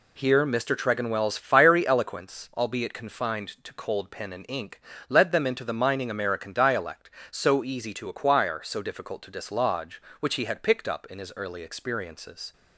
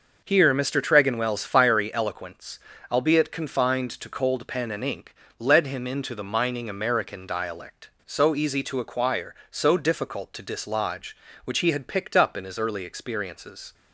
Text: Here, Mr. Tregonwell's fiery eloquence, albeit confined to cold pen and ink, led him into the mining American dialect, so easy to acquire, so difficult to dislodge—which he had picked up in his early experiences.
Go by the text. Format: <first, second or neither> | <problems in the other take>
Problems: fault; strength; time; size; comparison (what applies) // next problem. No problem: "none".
second | says "them" for "him"; at 5.3 s